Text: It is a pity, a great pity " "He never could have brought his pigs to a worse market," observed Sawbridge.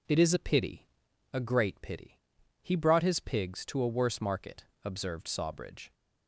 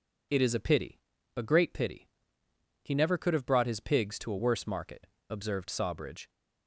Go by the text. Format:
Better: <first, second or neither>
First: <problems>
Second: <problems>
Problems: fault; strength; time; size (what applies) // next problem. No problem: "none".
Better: second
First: skips "never could have"; at 2.7 s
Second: none